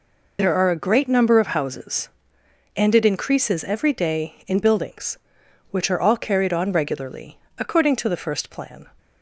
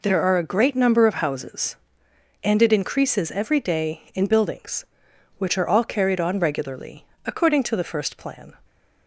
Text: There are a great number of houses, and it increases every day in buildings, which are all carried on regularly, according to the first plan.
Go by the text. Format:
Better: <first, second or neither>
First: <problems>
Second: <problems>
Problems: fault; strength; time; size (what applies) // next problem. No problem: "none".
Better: second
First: loses the start of "There"; at 0.3 s; 40 ms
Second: none